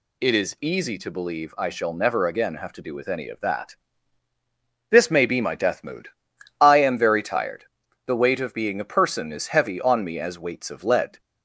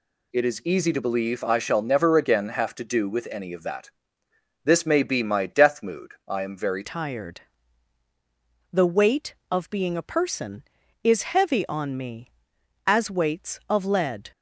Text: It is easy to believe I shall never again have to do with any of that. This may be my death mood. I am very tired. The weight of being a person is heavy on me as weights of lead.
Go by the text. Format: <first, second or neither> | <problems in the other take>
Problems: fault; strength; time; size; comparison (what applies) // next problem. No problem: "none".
first | changes voice at "tired"; from 6.8 s on; 7.5 s long